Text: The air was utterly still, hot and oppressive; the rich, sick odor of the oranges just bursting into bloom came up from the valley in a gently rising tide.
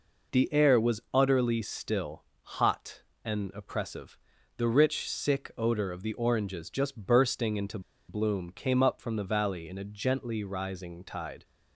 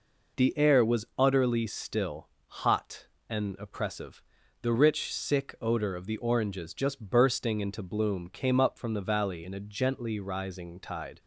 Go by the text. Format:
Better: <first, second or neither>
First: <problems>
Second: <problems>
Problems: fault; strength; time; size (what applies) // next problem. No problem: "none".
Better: second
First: pauses between "into" and "bloom"; slight; at 7.7 s; 0.29 s long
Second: none